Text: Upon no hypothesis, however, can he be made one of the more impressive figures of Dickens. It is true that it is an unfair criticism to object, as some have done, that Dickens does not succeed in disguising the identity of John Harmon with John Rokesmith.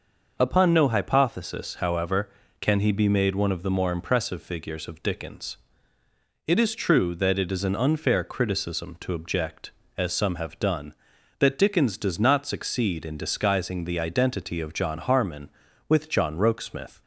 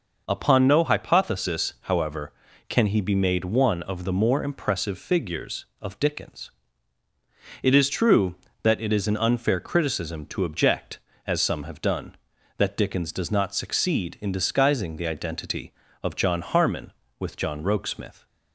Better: neither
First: none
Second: none

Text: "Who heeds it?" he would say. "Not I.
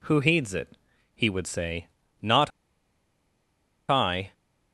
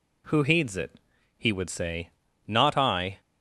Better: second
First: pauses between "Not" and "I"; strong; at 2.5 s; 1.3 s long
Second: none

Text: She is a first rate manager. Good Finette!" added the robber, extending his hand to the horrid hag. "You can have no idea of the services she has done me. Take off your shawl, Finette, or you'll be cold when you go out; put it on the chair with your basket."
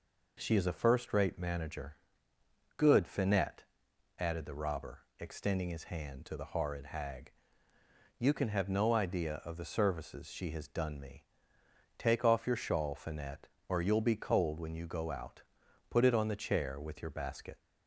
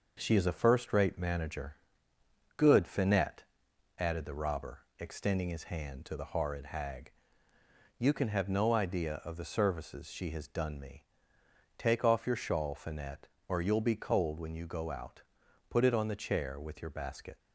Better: first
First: none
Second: gets quieter; throughout; 3.5 dB

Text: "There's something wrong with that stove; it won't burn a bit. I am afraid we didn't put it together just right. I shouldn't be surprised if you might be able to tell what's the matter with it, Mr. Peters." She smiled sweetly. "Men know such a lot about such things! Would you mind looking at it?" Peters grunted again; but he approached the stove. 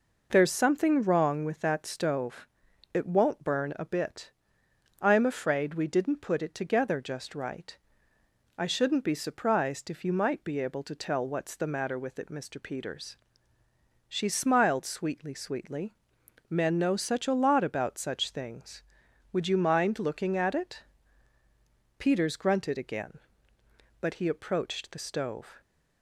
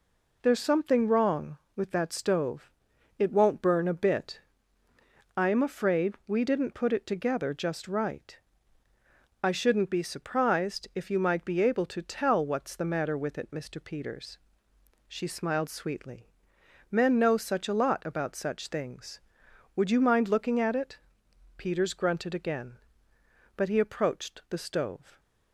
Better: second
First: says "sweetly" twice; at 15.3 s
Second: none

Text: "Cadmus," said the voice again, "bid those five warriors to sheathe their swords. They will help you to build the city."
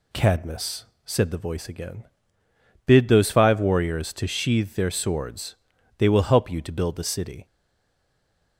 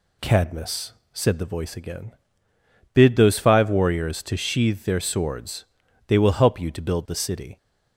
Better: second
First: stays silent after the last word; from 7.4 s on; 1.1 s long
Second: none

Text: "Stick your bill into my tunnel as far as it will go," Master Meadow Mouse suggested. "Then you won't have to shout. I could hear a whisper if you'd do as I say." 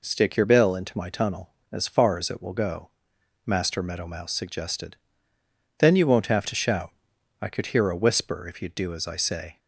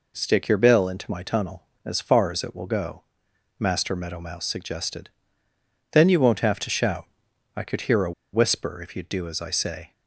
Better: first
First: none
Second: pauses between "a" and "whisper"; slight; at 8.1 s; 0.22 s long

